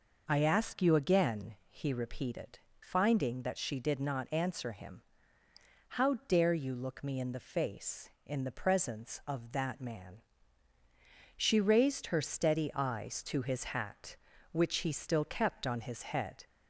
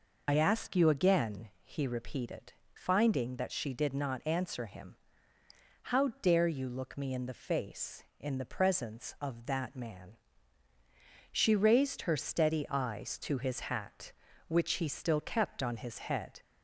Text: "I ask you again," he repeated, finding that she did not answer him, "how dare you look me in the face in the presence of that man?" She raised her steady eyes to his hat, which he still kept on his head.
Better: first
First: none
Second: loses the start of "I"; at 0.2 s; 45 ms

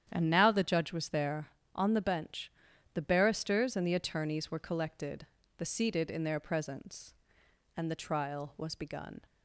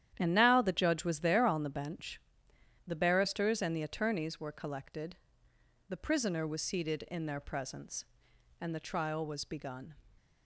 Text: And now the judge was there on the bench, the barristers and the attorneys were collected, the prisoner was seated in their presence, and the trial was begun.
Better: second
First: starts louder than the rest; strong; until 1.1 s; 9.5 dB // skips "prisoner was"; at 5.6 s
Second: starts louder than the rest; strong; until 1.1 s; 10.5 dB

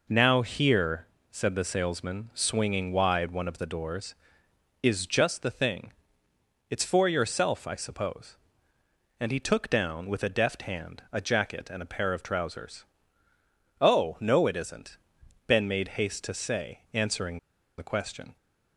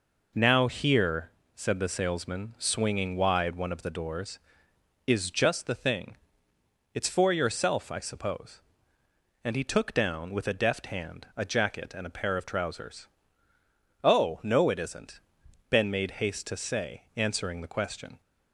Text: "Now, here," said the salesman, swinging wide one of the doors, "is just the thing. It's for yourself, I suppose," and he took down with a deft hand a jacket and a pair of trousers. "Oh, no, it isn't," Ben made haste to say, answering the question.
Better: second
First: pauses between "answering" and "the"; at 17.3 s; 0.40 s long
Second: none

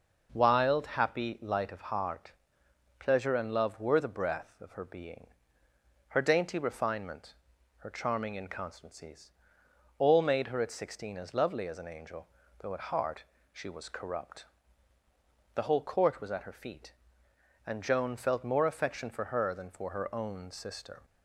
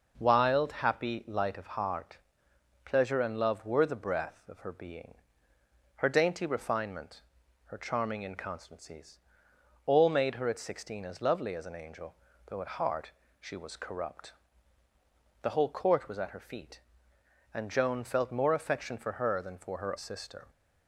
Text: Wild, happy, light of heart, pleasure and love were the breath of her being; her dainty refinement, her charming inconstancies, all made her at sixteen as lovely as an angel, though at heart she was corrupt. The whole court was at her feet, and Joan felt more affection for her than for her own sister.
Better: first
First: pauses between "heart" and "she"; slight; at 13.2 s; 0.32 s long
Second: pauses between "heart" and "she"; slight; at 13.1 s; 0.32 s long // skips "own"; at 19.9 s

